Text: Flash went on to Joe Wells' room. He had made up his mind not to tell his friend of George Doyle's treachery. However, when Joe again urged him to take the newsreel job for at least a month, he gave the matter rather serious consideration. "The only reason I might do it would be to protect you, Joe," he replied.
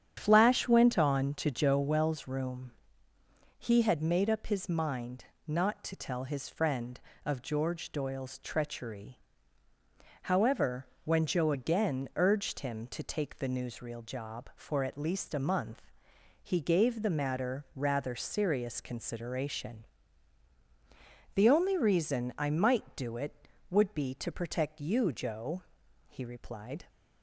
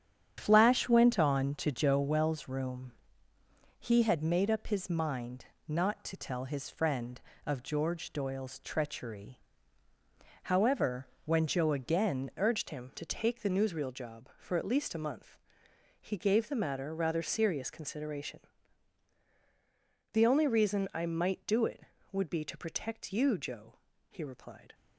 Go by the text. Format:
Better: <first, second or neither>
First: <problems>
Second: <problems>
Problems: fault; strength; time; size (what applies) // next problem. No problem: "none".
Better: first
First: starts louder than the rest; strong; until 1.1 s; 9 dB // pauses between "mind" and "not"; slight; at 5.2 s; 0.20 s long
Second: starts louder than the rest; strong; until 1.3 s; 9 dB // pauses between "mind" and "not"; slight; at 5.4 s; 0.20 s long // changes voice at "urged"; from 12.3 s on; 12.4 s long